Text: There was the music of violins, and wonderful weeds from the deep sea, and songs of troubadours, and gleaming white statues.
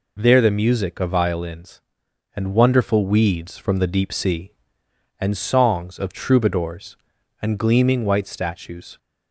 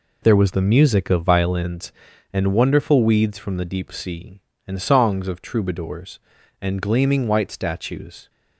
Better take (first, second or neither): second